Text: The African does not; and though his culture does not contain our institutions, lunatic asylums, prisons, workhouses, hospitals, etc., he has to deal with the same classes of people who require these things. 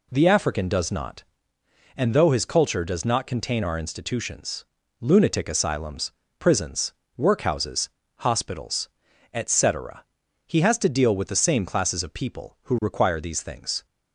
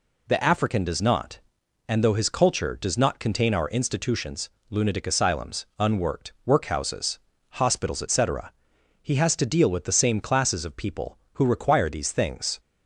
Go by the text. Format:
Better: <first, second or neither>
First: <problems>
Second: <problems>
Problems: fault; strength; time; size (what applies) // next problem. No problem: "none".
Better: first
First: none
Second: says "unworked" for "prisons"; at 5.7 s